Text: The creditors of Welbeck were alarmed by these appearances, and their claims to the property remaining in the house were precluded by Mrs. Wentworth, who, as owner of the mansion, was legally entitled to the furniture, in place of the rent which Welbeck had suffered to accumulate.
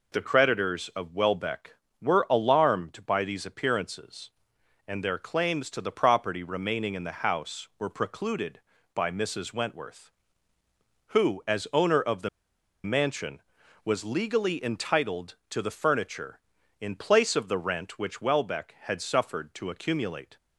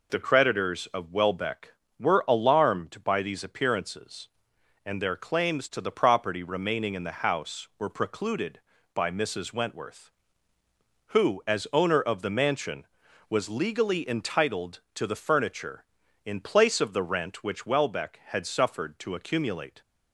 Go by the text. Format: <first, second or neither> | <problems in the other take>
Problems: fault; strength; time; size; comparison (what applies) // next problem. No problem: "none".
second | pauses between "the" and "mansion"; noticeable; at 12.2 s; 0.55 s long